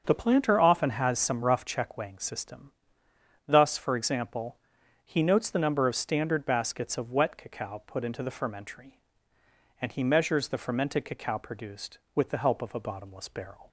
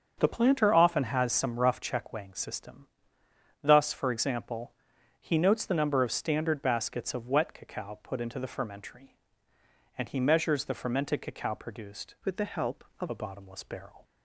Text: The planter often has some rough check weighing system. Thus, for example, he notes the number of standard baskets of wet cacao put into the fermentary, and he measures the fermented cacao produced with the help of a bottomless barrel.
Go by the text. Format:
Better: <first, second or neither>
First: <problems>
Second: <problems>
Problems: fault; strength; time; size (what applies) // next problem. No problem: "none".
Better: first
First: starts louder than the rest; until 1.0 s; 6.5 dB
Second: starts louder than the rest; until 1.1 s; 7 dB // changes voice from "with" to "of"; from 12.2 to 13.0 s; 0.8 s long